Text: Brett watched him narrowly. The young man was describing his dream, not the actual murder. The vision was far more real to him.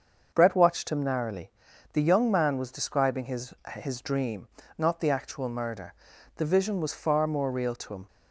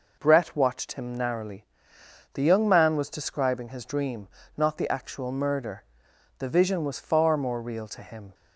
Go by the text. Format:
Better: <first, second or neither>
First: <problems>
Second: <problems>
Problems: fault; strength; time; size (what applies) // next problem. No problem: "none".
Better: second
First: starts louder than the rest; until 1.3 s; 6.5 dB // says "his" twice; at 3.7 s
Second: none